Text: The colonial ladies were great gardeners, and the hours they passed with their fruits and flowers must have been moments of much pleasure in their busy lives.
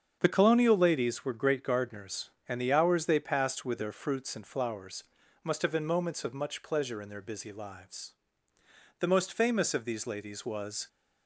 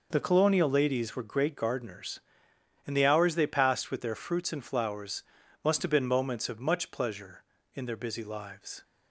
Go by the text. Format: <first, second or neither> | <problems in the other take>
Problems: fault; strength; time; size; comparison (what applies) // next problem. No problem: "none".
second | starts louder than the rest; strong; until 1.2 s; 7.5 dB // pauses between "flowers" and "must"; at 5.0 s; 0.40 s long; also in the second // goes on to say "The most famous of these ladies was"; strong; from 8.9 s on; 1.9 s long